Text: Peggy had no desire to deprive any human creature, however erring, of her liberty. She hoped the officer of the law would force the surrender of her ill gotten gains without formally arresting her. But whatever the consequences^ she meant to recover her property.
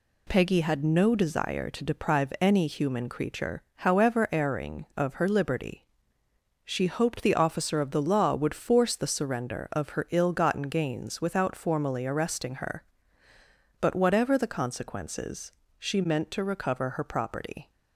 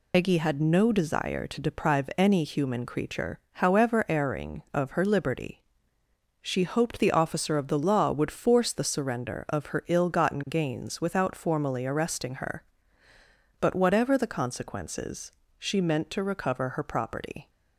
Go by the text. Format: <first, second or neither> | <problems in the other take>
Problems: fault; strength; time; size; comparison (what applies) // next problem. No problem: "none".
first | loses the start of "Peggy"; at 0.1 s; 110 ms // pauses between "consequences" and "she"; slight; at 15.3 s; 0.26 s long; slight in the first